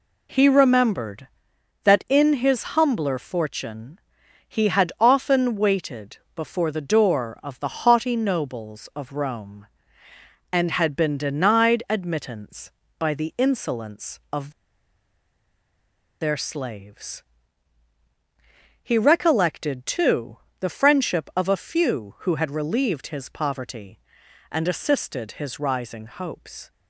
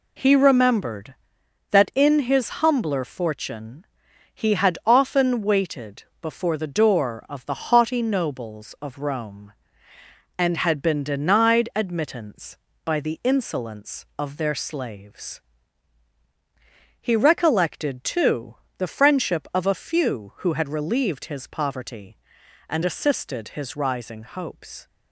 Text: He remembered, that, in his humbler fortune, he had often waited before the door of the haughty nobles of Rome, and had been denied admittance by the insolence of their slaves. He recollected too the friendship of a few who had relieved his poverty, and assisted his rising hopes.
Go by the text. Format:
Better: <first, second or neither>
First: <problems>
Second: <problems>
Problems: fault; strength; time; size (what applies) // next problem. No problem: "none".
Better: second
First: pauses between "waited" and "before"; slight; at 6.1 s; 0.18 s long // pauses between "of" and "their"; strong; at 14.5 s; 1.6 s long // pauses between "too" and "the"; slight; at 20.3 s; 0.24 s long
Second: pauses between "waited" and "before"; slight; at 6.0 s; 0.18 s long // pauses between "too" and "the"; slight; at 18.5 s; 0.24 s long